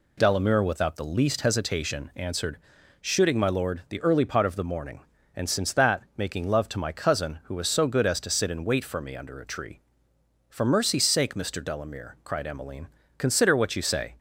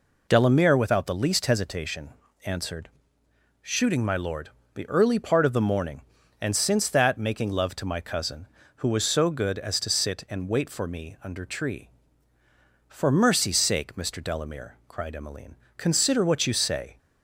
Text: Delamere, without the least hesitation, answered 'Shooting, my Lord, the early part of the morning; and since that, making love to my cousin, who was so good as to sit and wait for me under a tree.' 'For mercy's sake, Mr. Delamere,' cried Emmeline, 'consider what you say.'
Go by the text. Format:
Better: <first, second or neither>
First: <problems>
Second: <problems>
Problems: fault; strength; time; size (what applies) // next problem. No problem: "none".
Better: first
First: pauses between "answered" and "Shooting"; at 2.5 s; 0.44 s long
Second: pauses between "answered" and "Shooting"; noticeable; at 2.8 s; 0.72 s long // skips "a"; at 11.4 s